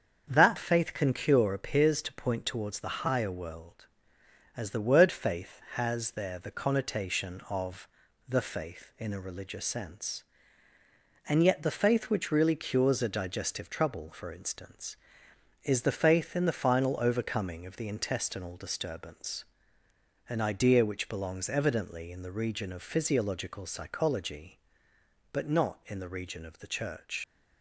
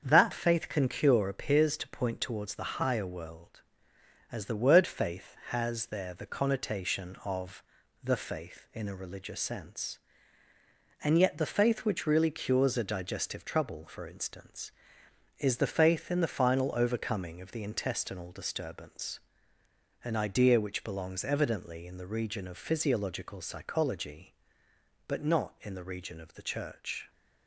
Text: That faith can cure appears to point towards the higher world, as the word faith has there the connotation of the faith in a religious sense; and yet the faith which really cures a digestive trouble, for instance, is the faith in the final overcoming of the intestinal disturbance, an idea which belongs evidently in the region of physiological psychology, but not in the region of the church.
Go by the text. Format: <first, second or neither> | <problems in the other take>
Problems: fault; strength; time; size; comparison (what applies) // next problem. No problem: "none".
second | starts louder than the rest; until 1.2 s; 7 dB; also in the second // pauses between "of" and "the"; at 7.8 s; 0.40 s long; also in the second // leaves "church" unfinished; at 27.2 s; 105 ms